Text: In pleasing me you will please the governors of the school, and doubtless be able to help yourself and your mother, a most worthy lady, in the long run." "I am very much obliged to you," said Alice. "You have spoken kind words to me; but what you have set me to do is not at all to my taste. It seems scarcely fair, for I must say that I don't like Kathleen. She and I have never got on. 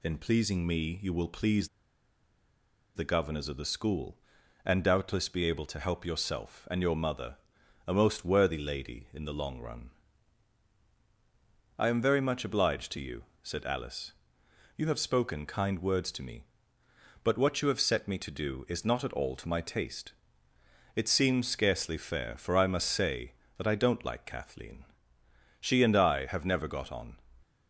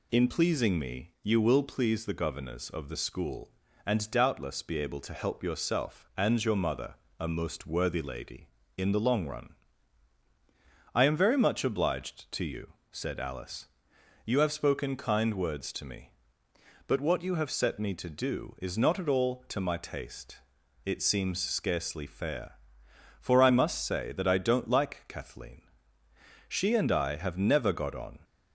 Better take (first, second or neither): second